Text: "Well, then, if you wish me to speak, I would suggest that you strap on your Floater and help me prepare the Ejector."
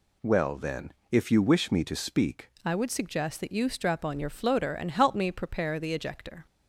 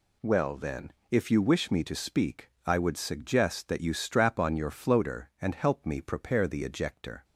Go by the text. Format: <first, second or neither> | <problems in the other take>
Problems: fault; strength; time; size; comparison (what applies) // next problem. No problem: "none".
second | changes voice at "I"; from 2.6 s on; 3.8 s long